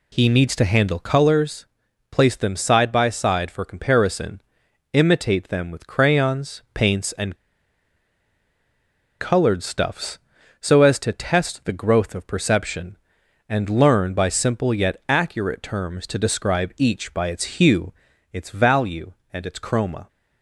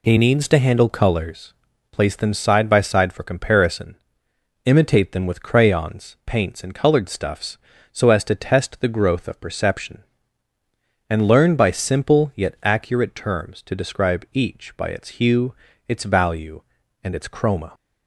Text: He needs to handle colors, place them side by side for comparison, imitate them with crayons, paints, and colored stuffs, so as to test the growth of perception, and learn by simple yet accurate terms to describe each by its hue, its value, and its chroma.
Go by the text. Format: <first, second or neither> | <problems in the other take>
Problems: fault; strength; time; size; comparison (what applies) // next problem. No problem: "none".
second | pauses between "and" and "colored"; strong; at 7.3 s; 1.8 s long